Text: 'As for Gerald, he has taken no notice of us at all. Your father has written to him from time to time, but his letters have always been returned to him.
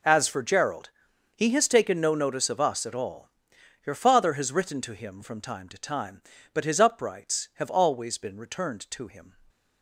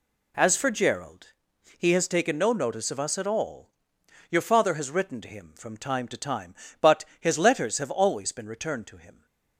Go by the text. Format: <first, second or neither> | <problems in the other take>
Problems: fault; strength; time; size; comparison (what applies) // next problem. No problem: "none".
second | says "uprights" for "letters"; at 6.8 s // stays silent after the last word; slight; from 9.2 s on; 0.6 s long